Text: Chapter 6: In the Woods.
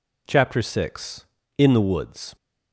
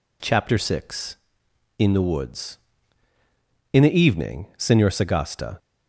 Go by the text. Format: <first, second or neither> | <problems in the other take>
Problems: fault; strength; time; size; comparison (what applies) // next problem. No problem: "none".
first | goes on to say "In the evening Senor Sagasta"; strong; from 3.7 s on; 1.8 s long